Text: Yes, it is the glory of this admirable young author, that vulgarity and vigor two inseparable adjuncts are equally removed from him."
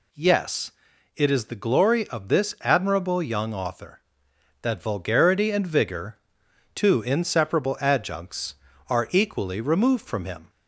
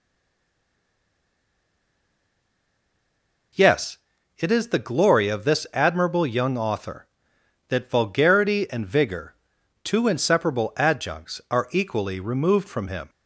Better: first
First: pauses between "vigor" and "two"; noticeable; at 6.1 s; 0.58 s long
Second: stays silent before the first word; strong; until 3.5 s; 3.5 s long // pauses between "vigor" and "two"; noticeable; at 9.3 s; 0.48 s long

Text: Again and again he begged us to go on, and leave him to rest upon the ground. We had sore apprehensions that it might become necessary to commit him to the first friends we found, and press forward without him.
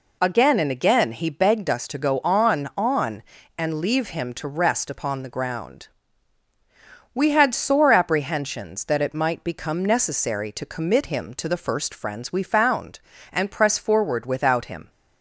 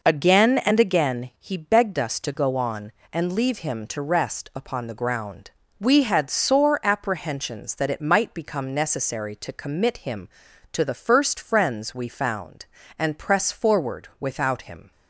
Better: second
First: says "on" twice; at 2.7 s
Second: none

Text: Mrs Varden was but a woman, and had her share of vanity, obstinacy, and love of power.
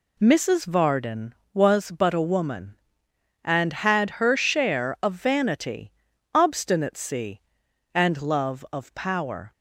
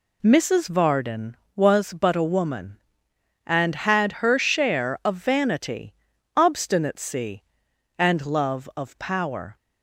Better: neither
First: none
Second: none

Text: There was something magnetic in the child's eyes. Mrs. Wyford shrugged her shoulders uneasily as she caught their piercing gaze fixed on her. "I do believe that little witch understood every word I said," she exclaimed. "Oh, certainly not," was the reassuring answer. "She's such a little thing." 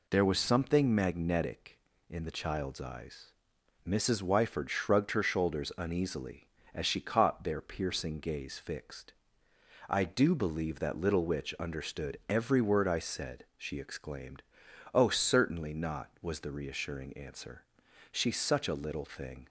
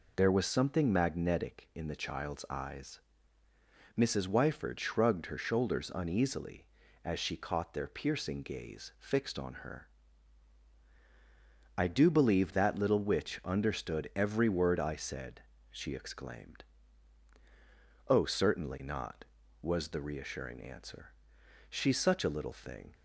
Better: second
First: skips "on her"; at 9.5 s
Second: none

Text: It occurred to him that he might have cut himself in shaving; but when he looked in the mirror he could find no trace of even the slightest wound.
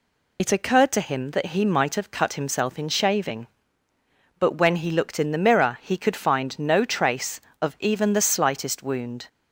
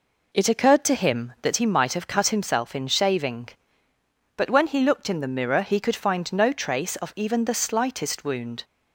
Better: second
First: loses the start of "It"; at 0.3 s; 65 ms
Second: none

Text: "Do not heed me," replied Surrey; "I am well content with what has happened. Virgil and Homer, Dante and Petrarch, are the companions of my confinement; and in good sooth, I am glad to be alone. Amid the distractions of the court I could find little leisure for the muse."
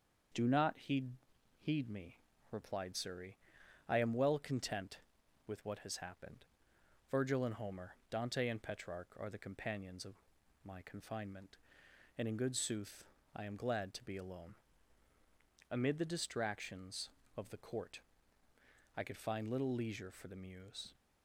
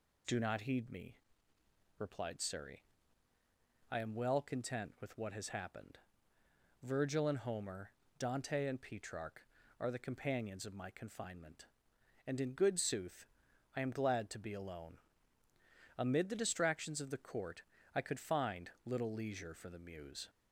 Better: second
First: starts louder than the rest; until 1.7 s; 6.5 dB // says "heed" twice; at 1.5 s // pauses between "of" and "my"; noticeable; at 10.1 s; 0.50 s long // pauses between "court" and "I"; noticeable; at 18.0 s; 0.96 s long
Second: pauses between "court" and "I"; slight; at 17.6 s; 0.32 s long

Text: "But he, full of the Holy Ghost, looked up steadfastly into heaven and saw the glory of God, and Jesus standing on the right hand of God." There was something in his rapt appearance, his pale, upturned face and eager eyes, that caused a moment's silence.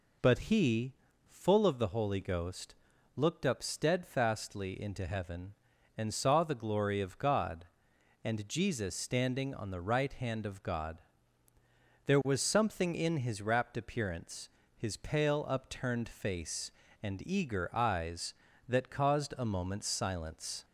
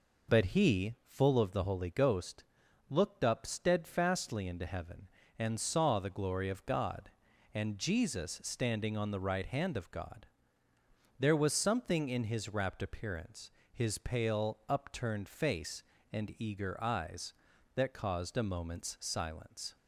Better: neither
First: none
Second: none

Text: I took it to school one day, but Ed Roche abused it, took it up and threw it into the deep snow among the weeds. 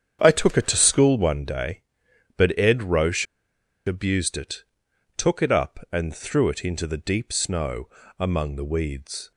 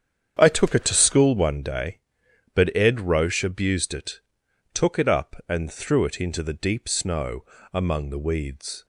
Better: second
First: starts louder than the rest; strong; until 1.2 s; 8.5 dB // pauses between "Roche" and "abused"; noticeable; at 3.2 s; 0.61 s long // pauses between "snow" and "among"; slight; at 7.8 s; 0.32 s long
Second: starts louder than the rest; strong; until 1.4 s; 8.5 dB // pauses between "snow" and "among"; slight; at 7.4 s; 0.30 s long

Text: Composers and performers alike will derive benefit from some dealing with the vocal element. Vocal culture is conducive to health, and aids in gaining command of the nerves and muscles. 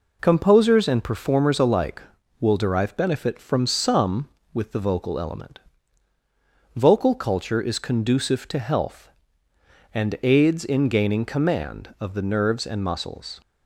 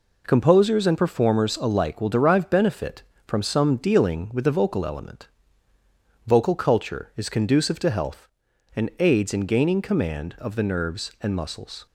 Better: second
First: skips "dealing"; at 4.4 s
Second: none

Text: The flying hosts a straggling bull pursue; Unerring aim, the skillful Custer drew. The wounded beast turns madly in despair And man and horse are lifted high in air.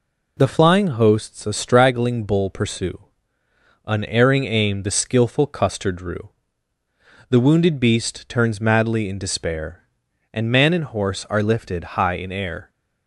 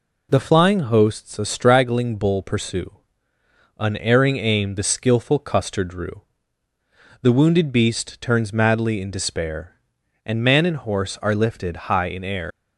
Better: first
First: none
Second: leaves "air" unfinished; at 12.5 s; 115 ms

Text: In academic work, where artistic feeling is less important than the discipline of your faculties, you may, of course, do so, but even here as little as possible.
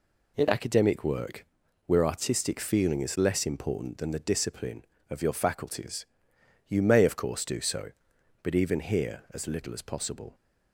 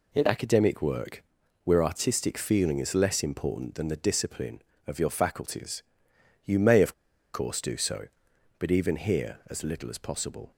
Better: first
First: none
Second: pauses between "of" and "course"; at 6.9 s; 0.41 s long

